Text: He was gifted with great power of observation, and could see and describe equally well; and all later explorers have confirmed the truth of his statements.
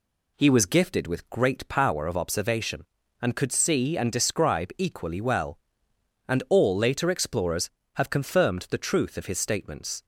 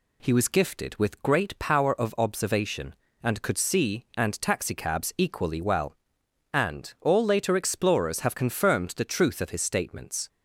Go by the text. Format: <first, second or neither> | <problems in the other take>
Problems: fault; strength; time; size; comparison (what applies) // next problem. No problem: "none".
first | says "taxicabs" for "describe"; at 4.3 s